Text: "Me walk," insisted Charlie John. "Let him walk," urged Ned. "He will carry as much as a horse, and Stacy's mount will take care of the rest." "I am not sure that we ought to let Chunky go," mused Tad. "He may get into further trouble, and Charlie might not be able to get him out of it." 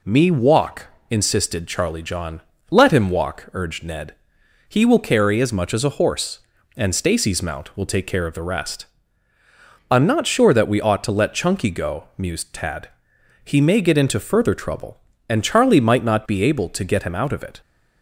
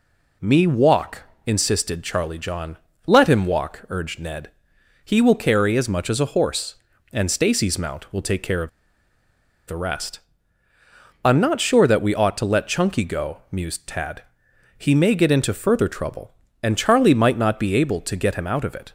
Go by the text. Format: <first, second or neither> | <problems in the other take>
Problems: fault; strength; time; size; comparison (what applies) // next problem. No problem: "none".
first | pauses between "of" and "the"; at 8.6 s; 0.98 s long